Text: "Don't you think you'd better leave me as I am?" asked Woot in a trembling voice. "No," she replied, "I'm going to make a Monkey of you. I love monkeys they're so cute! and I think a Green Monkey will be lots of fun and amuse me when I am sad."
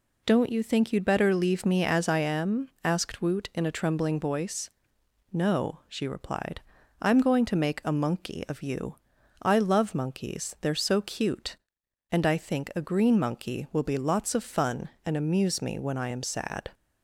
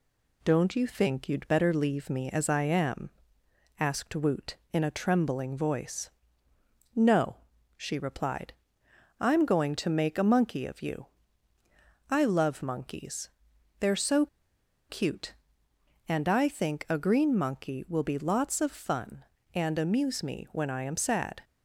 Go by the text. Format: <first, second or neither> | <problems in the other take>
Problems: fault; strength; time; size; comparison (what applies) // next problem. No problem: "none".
first | pauses between "monkeys" and "they're"; noticeable; at 13.2 s; 0.52 s long // pauses between "so" and "cute"; noticeable; at 14.2 s; 0.64 s long